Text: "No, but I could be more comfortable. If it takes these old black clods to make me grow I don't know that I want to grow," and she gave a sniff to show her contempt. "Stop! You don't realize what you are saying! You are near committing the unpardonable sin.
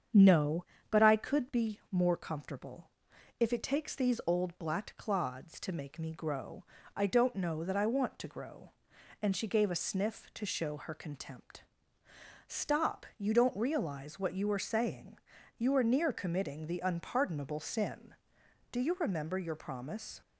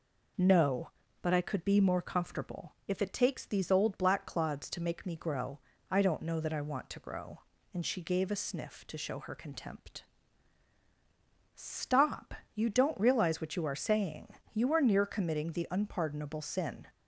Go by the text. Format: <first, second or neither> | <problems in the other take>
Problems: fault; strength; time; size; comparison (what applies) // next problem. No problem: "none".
second | starts louder than the rest; strong; until 1.3 s; 7.5 dB // pauses between "grow" and "I"; slight; at 6.6 s; 0.32 s long; slight in the second // goes on to say "Do you remember your promise"; from 18.6 s on; 1.5 s long